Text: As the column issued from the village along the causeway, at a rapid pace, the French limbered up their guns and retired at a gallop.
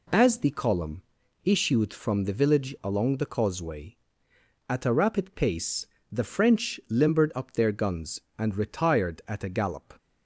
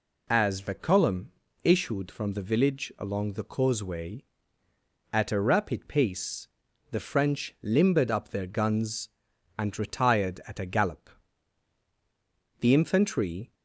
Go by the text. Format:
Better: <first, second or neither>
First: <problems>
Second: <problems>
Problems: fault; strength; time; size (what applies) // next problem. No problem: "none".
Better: first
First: pauses between "column" and "issued"; at 1.0 s; 0.42 s long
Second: pauses between "column" and "issued"; slight; at 1.3 s; 0.32 s long // goes on to say "The infantry"; noticeable; from 12.5 s on; 0.94 s long